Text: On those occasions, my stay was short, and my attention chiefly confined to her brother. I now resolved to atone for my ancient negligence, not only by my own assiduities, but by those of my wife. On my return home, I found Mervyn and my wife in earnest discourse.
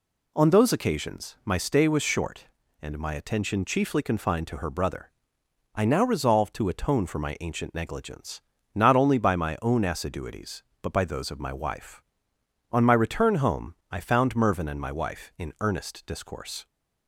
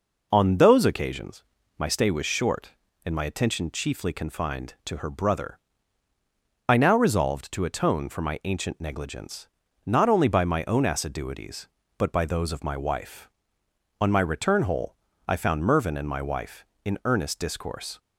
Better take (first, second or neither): first